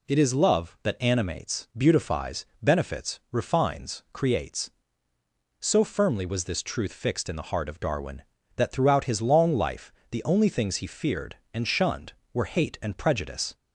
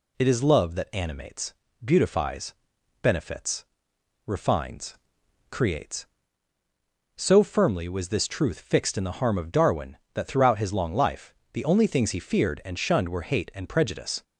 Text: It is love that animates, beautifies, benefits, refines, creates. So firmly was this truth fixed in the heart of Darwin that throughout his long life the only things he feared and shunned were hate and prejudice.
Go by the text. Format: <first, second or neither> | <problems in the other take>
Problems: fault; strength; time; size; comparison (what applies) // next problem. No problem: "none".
first | says "harm" for "heart"; at 9.1 s // pauses between "life" and "the"; slight; at 11.3 s; 0.16 s long; slight in the first